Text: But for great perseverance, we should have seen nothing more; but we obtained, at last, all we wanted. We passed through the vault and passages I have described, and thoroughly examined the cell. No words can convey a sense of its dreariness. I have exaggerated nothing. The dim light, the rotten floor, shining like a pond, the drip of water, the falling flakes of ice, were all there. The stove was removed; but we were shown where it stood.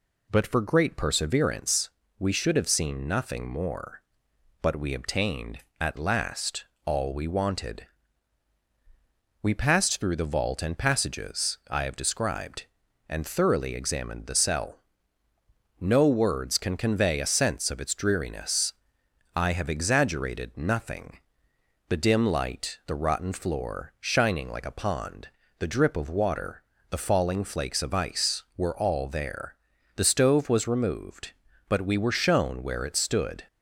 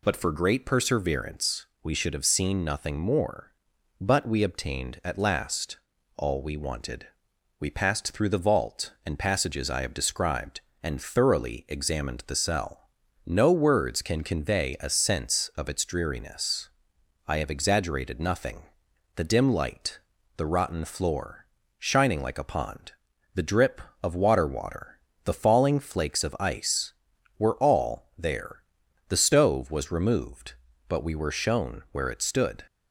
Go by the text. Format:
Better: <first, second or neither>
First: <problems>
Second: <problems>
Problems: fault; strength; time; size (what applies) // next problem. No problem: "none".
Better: first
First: none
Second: says "water" twice; at 24.4 s